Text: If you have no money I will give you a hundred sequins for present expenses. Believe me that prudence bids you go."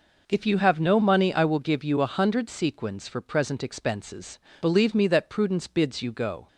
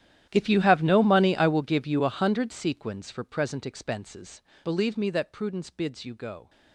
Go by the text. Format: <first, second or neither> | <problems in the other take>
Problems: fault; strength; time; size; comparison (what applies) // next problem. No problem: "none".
first | gets quieter; strong; throughout; 19.5 dB